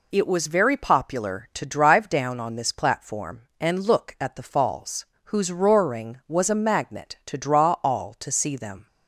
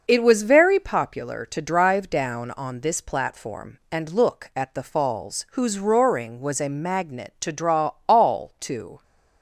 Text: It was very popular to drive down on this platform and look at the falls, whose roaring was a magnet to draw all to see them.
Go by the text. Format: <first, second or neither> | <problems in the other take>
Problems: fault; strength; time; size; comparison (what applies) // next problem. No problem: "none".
first | pauses between "draw" and "all"; slight; at 7.9 s; 0.16 s long // stops before "see them"; at 9.0 s